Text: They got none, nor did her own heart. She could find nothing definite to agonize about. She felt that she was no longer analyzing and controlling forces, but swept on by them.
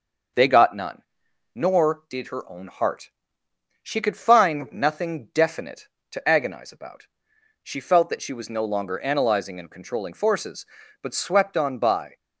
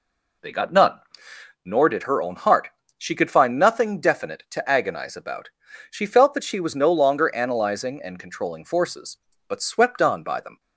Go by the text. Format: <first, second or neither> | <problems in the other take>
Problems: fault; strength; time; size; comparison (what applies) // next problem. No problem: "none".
second | starts louder than the rest; until 1.8 s; 6.5 dB // stops before "them"; at 12.1 s